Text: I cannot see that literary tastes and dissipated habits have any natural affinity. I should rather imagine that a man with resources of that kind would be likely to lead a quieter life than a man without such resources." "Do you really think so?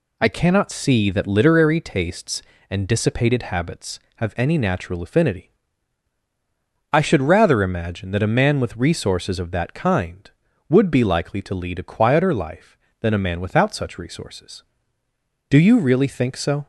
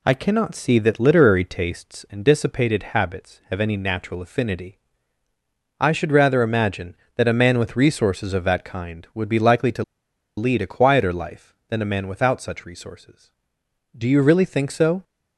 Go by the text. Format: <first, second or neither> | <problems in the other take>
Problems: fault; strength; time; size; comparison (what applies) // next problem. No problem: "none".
first | pauses between "to" and "lead"; noticeable; at 9.8 s; 0.53 s long